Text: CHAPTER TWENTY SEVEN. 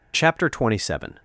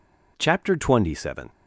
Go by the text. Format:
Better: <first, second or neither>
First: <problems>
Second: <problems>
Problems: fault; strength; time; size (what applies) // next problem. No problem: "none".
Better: neither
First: none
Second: none